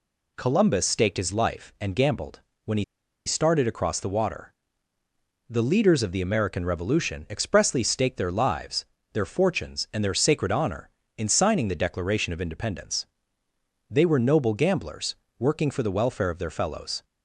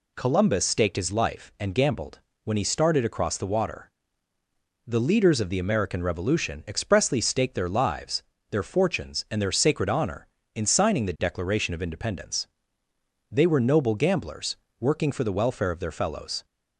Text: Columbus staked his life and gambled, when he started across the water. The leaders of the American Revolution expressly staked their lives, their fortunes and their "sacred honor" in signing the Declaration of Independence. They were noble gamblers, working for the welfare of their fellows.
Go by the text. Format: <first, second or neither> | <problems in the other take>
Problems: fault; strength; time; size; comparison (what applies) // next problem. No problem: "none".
second | pauses between "he" and "started"; at 2.8 s; 0.41 s long